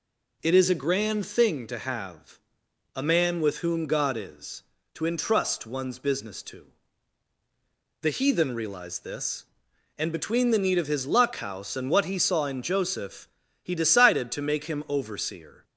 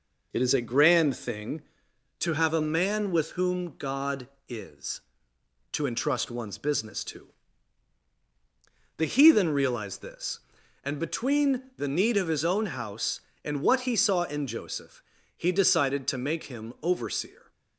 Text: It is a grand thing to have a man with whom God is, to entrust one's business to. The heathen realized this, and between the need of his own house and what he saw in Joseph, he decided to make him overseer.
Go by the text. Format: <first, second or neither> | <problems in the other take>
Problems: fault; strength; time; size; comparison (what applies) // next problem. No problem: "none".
second | pauses between "have" and "a"; noticeable; at 2.3 s; 0.56 s long // says "luck" for "own"; at 11.0 s